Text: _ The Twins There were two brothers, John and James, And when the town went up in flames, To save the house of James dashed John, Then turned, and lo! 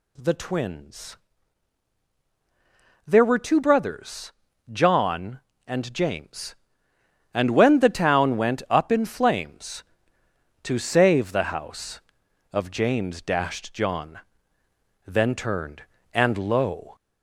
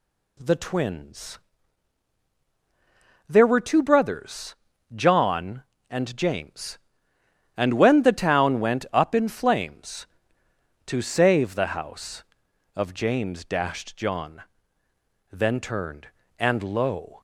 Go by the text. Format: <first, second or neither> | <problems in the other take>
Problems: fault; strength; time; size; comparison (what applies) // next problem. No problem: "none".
second | gets louder; slight; throughout; 2 dB // pauses between "Twins" and "There"; strong; at 1.1 s; 1.8 s long; strong in the second